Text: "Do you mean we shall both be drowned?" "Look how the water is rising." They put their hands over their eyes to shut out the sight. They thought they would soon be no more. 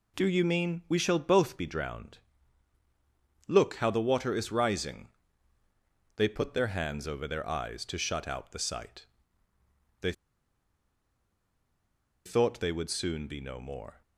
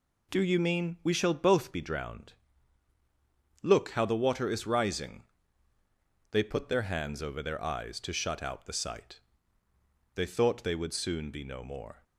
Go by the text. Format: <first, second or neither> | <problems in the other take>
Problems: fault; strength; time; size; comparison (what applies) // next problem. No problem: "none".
second | pauses between "They" and "thought"; strong; at 10.1 s; 2.1 s long